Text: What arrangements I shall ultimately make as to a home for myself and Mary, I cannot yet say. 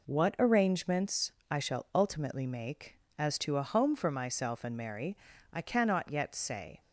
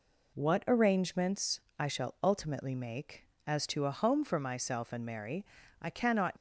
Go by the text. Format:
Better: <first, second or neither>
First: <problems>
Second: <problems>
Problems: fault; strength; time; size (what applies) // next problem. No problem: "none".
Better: first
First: pauses between "arrangements" and "I"; slight; at 1.3 s; 0.18 s long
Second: pauses between "arrangements" and "I"; slight; at 1.5 s; 0.18 s long // stops before "yet say"; at 6.3 s